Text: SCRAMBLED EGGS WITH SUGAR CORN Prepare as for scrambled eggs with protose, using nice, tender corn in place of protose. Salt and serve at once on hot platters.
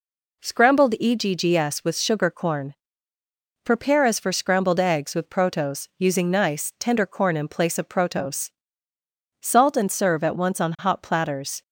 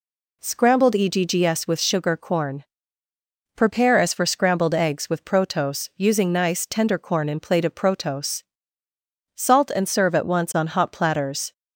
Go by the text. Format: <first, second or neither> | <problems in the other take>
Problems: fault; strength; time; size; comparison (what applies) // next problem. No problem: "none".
first | pauses between "CORN" and "Prepare"; noticeable; at 2.6 s; 0.94 s long; noticeable in the first // says "plate" for "place"; at 7.4 s